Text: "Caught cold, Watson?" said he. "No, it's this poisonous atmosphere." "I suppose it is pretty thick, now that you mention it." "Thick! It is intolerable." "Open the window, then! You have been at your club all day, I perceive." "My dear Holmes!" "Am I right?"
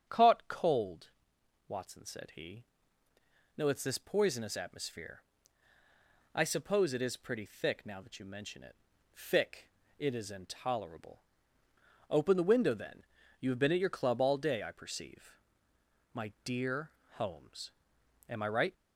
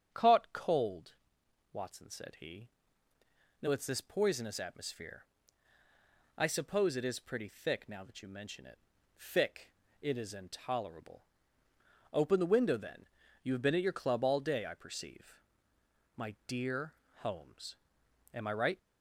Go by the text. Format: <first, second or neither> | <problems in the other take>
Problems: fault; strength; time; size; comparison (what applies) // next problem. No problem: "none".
neither | starts louder than the rest; strong; the same in both // pauses between "dear" and "Holmes"; slight; the same in both